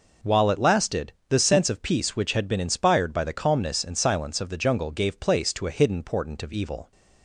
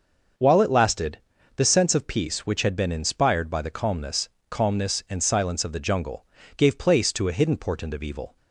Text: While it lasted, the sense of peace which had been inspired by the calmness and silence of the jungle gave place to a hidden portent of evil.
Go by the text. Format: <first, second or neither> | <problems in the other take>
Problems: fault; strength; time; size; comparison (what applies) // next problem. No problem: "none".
first | starts louder than the rest; until 1.7 s; 6 dB // says "calmness" twice; at 4.4 s // pauses between "jungle" and "gave"; slight; at 6.2 s; 0.32 s long